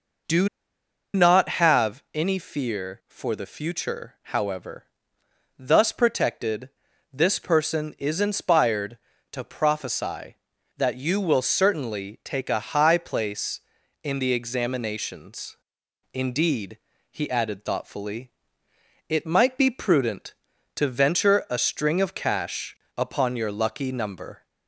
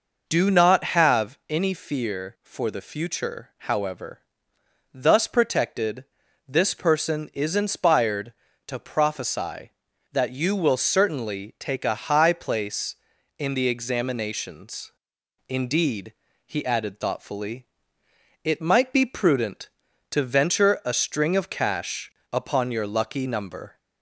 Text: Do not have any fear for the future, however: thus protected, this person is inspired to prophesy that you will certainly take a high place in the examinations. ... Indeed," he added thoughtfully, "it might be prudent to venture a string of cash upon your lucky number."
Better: second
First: pauses between "Do" and "not"; noticeable; at 0.4 s; 0.66 s long // pauses between "cash" and "upon"; slight; at 22.7 s; 0.22 s long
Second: pauses between "cash" and "upon"; slight; at 22.0 s; 0.22 s long

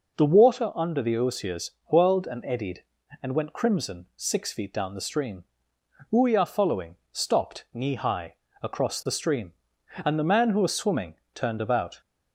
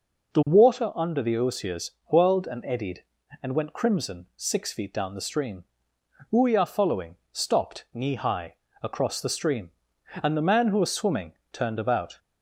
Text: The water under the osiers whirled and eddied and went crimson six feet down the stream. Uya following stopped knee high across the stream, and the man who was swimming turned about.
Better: neither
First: pauses between "osiers" and "whirled"; slight; at 1.7 s; 0.16 s long // pauses between "following" and "stopped"; slight; at 6.9 s; 0.16 s long // pauses between "high" and "across"; slight; at 8.3 s; 0.26 s long // pauses between "swimming" and "turned"; slight; at 11.1 s; 0.20 s long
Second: pauses between "osiers" and "whirled"; slight; at 1.9 s; 0.16 s long // pauses between "following" and "stopped"; slight; at 7.1 s; 0.16 s long // pauses between "high" and "across"; slight; at 8.5 s; 0.26 s long // pauses between "swimming" and "turned"; slight; at 11.3 s; 0.20 s long

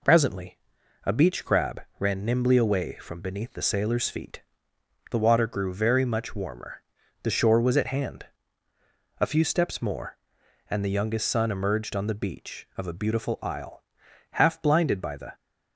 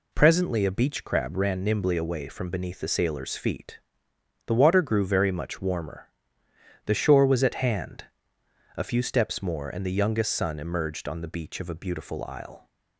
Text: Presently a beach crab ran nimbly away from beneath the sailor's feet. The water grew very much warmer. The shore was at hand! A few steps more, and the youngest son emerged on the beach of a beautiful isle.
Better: second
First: pauses between "Presently" and "a"; noticeable; at 0.5 s; 0.46 s long // pauses between "crab" and "ran"; slight; at 1.7 s; 0.20 s long // goes on to say "Half blinded by the"; noticeable; from 14.3 s on; 1.0 s long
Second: none

